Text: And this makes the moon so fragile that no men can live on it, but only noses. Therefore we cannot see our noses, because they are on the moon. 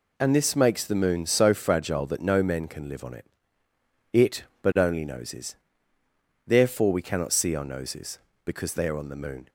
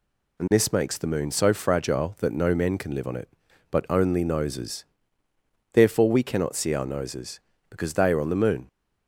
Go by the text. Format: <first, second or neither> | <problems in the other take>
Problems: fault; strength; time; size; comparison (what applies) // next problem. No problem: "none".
second | says "it" twice; at 4.1 s